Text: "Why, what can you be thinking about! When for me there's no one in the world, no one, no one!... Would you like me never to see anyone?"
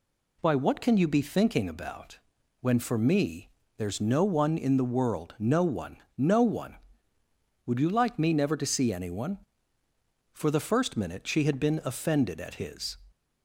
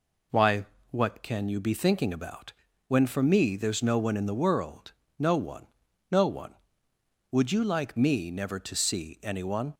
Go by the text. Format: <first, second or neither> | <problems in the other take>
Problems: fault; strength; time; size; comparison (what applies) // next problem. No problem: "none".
second | pauses between "me" and "there's"; slight; at 3.4 s; 0.28 s long // goes on to say "For the first minute she had been offended at his"; strong; from 10.3 s on; 2.6 s long